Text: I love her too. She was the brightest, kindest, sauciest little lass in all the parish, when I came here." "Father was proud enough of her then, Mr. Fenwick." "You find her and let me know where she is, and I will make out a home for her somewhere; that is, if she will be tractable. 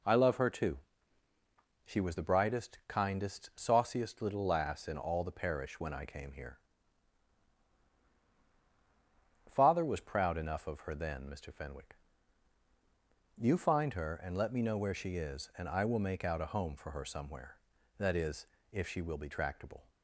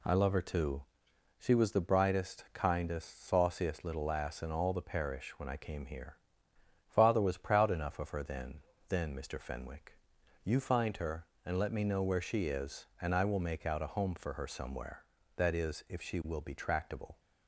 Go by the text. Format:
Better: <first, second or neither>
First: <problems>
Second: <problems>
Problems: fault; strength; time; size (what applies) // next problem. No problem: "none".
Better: first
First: none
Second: says "then" twice; at 8.8 s